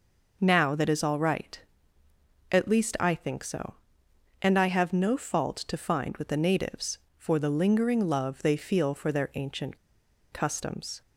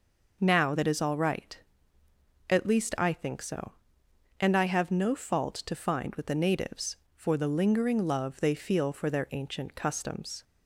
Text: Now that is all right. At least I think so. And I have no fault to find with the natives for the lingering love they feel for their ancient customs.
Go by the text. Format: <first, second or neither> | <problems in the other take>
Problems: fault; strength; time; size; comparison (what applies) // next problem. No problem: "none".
second | pauses between "ancient" and "customs"; noticeable; at 9.7 s; 0.55 s long